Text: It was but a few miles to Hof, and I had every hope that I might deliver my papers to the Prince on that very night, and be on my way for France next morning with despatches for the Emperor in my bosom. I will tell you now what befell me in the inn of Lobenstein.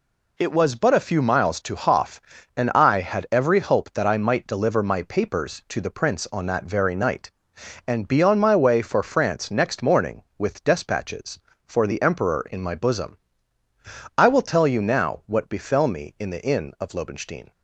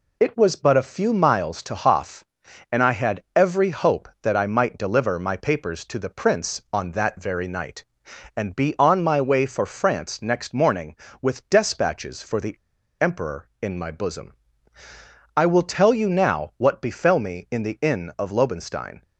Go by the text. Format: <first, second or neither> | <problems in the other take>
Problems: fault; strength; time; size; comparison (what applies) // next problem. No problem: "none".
first | pauses between "the" and "Emperor"; noticeable; at 12.5 s; 0.48 s long